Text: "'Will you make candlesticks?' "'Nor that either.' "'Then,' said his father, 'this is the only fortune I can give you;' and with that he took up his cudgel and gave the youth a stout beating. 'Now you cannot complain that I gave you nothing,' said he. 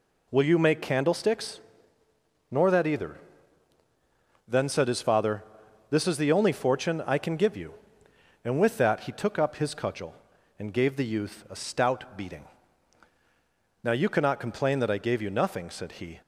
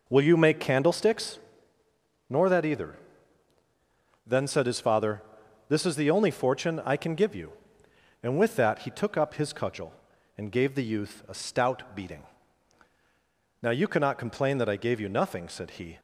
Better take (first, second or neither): first